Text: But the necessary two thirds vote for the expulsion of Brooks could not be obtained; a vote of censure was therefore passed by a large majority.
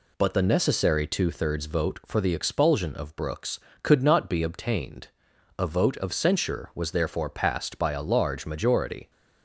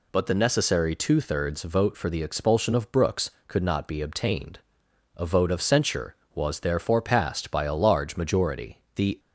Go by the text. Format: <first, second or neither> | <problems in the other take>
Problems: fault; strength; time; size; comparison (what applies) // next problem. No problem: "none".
first | goes on to say "The"; slight; from 8.9 s on; 0.24 s long